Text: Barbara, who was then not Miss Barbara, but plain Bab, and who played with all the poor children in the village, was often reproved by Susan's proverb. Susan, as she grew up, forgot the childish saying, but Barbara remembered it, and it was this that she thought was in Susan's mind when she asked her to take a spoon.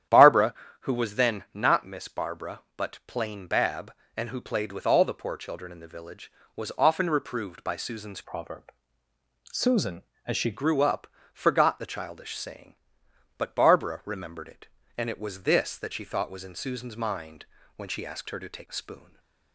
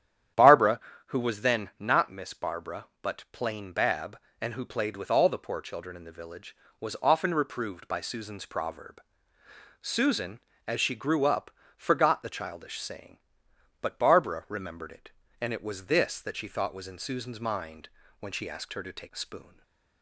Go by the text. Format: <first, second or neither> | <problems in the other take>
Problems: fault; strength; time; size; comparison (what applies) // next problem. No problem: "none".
second | starts louder than the rest; strong; until 1.3 s; 10.5 dB; strong in the second // changes voice from "proverb" to "she"; from 8.2 to 10.5 s; 2.3 s long // pauses between "mind" and "when"; slight; at 17.4 s; 0.32 s long; slight in the second // stays silent after the last word; slight; from 18.9 s on; 0.6 s long; slight in the second